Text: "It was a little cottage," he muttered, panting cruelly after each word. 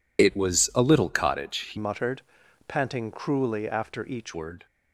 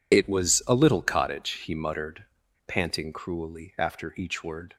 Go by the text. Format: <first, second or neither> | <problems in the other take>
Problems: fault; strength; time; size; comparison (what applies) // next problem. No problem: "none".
second | changes voice from "muttered" to "each"; from 1.7 to 4.3 s; 2.6 s long